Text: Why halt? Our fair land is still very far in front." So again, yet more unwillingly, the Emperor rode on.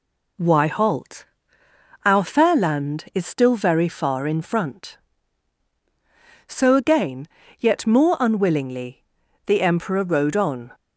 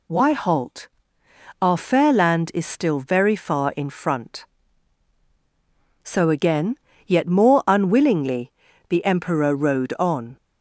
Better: neither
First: none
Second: none

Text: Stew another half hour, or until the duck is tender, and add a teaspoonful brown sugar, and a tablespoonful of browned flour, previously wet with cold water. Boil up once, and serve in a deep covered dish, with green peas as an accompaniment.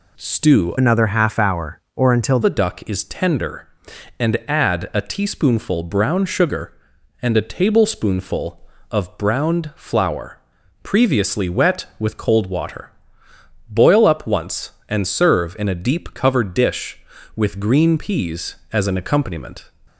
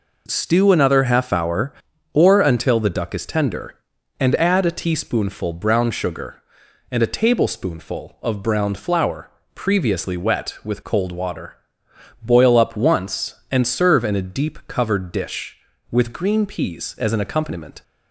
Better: second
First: changes voice from "another" to "until"; from 0.7 to 2.3 s; 1.6 s long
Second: none

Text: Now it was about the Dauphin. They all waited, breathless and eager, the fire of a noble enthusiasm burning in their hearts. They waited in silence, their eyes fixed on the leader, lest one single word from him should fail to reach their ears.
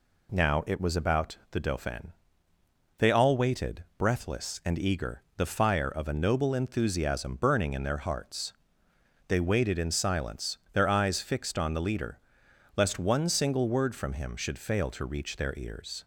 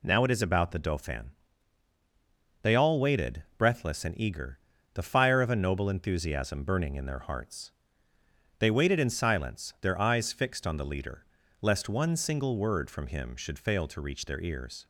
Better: first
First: none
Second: says "is" for "was"; at 0.3 s

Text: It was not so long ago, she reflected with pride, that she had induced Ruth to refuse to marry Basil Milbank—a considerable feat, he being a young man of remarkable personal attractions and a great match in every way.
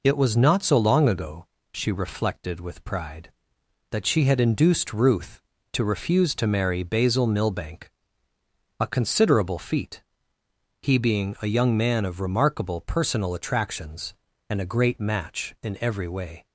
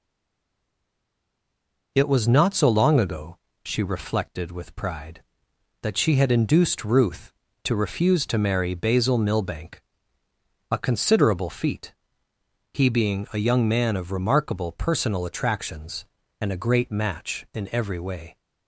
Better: first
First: none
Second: stays silent before the first word; noticeable; until 1.9 s; 1.9 s long

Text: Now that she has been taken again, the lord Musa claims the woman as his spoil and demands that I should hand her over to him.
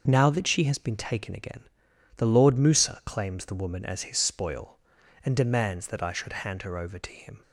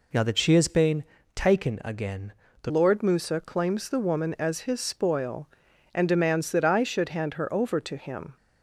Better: first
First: none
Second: pauses between "been" and "taken"; slight; at 1.0 s; 0.32 s long // changes voice at "lord"; from 2.6 s on; 5.7 s long

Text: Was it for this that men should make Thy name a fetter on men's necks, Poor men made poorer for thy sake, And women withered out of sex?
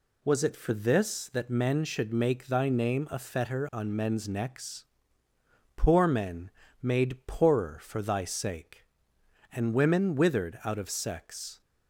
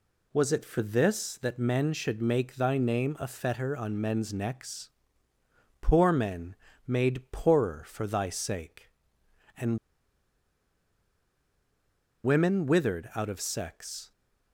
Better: first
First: pauses between "men" and "made"; slight; at 6.4 s; 0.32 s long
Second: pauses between "men" and "made"; slight; at 6.5 s; 0.32 s long // pauses between "And" and "women"; strong; at 9.7 s; 2.4 s long

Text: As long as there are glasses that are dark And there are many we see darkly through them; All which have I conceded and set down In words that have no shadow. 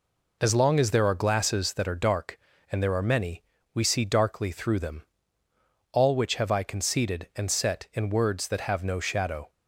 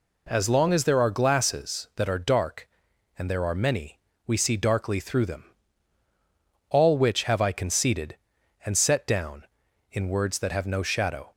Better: second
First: pauses between "many" and "we"; slight; at 3.4 s; 0.32 s long // skips "down"; at 7.9 s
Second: pauses between "many" and "we"; slight; at 3.9 s; 0.28 s long

